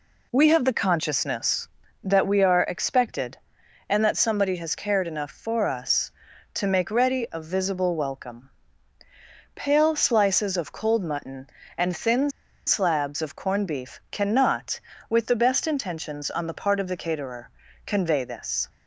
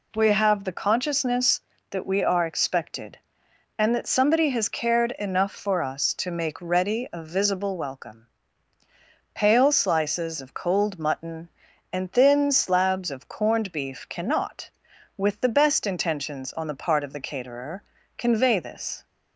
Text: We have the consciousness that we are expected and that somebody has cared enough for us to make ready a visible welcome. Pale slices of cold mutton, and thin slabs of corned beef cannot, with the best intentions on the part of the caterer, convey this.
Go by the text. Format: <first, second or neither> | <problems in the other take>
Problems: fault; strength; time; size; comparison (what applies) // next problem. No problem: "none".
second | pauses between "thin" and "slabs"; at 12.2 s; 0.37 s long